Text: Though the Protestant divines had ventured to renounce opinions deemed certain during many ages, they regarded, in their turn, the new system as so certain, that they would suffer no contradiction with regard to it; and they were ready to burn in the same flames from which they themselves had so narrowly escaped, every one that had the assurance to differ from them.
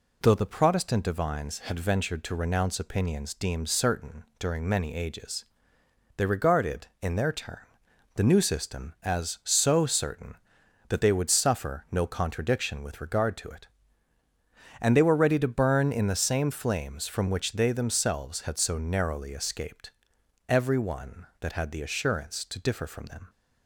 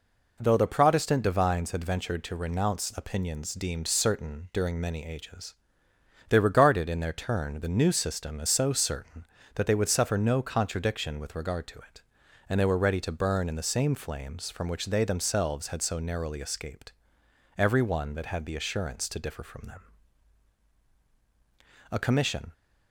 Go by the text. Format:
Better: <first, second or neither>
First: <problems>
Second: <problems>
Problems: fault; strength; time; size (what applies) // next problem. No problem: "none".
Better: first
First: none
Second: goes on to say "A commission"; noticeable; from 21.9 s on; 0.62 s long